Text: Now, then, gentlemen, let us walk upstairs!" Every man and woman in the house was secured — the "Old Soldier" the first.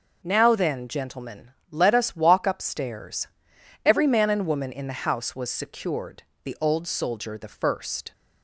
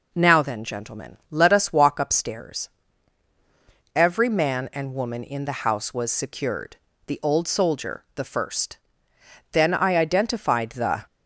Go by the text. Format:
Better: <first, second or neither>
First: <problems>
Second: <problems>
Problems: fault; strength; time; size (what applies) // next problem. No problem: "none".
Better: first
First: none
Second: goes on to say "Then I identified the"; from 9.5 s on; 1.5 s long